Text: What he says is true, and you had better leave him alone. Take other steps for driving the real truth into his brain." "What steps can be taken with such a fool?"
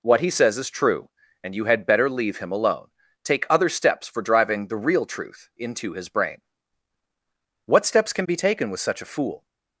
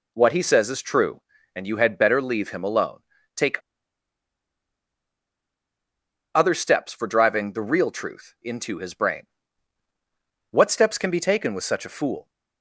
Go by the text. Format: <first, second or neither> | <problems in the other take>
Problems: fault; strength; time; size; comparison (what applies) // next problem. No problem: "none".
first | pauses between "Take" and "other"; strong; at 3.5 s; 2.7 s long